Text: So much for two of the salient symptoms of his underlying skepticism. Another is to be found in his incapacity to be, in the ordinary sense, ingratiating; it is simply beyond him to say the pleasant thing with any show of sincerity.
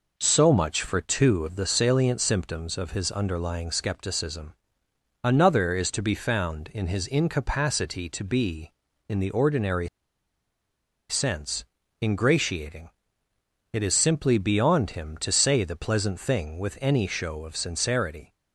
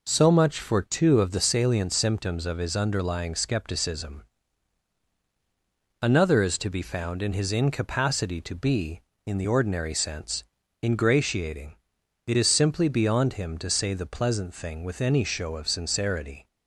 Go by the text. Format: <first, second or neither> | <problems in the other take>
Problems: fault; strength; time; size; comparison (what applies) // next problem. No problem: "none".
second | pauses between "ordinary" and "sense"; at 9.8 s; 1.2 s long